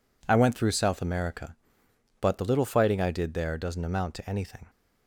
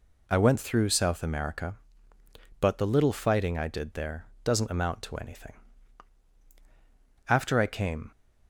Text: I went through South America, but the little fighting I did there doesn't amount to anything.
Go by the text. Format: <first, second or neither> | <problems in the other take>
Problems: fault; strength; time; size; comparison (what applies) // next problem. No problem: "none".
first | pauses between "there" and "doesn't"; slight; at 4.2 s; 0.18 s long // goes on to say "After I came"; noticeable; from 7.2 s on; 0.82 s long